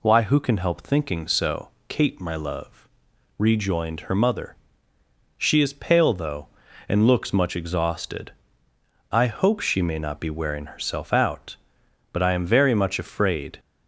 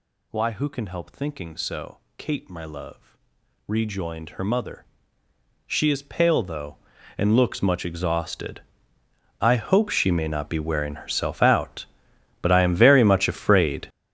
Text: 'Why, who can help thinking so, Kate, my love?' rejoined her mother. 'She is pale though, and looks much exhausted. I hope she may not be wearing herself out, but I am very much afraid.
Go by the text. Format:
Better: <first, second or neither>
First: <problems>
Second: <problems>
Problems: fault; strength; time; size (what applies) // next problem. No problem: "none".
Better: first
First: none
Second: gets louder; strong; throughout; 14 dB